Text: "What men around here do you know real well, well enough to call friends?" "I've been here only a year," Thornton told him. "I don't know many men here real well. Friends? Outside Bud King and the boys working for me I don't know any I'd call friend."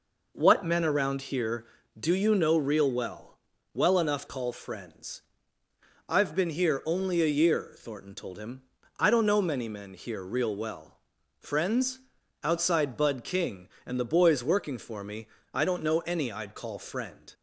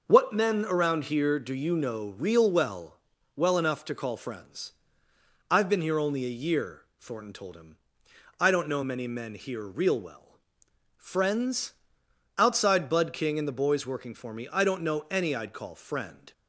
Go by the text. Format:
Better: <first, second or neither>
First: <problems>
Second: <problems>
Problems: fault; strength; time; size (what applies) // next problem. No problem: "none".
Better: second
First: skips "to"; at 4.2 s // pauses between "me" and "I"; slight; at 15.2 s; 0.30 s long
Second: none